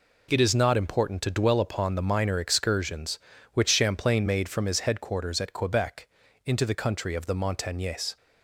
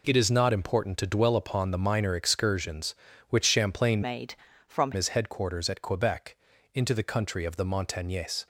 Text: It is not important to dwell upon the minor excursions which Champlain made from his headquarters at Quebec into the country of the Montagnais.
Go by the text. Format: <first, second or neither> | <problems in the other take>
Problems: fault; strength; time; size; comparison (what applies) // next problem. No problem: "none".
first | changes voice from "made" to "from"; from 4.0 to 4.9 s; 0.9 s long // pauses between "Quebec" and "into"; at 6.3 s; 0.38 s long; also in the first